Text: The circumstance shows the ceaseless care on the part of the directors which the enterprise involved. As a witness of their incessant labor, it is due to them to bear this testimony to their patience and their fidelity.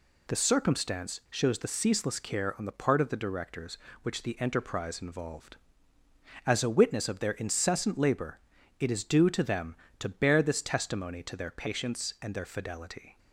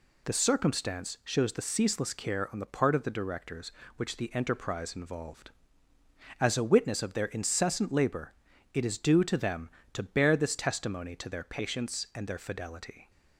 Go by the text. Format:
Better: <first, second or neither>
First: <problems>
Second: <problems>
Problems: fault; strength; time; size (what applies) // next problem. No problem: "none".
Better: neither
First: none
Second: none